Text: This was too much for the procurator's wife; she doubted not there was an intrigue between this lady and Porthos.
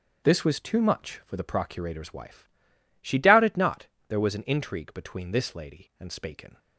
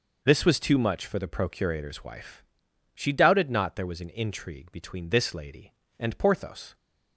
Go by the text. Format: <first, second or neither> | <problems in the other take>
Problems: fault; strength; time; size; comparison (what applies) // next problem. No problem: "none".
second | starts louder than the rest; strong; until 1.2 s; 7 dB // pauses between "not" and "there"; slight; at 3.8 s; 0.18 s long // says "Spaken" for "Porthos"; at 6.1 s